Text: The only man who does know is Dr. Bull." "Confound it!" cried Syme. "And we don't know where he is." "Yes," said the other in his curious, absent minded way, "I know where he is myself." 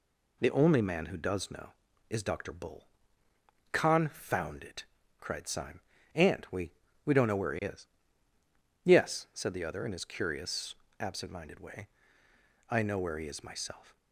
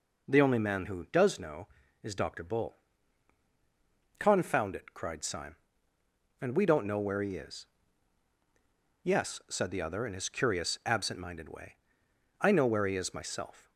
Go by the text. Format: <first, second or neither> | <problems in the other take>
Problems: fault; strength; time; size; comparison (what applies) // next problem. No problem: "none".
second | says "we" twice; at 7.0 s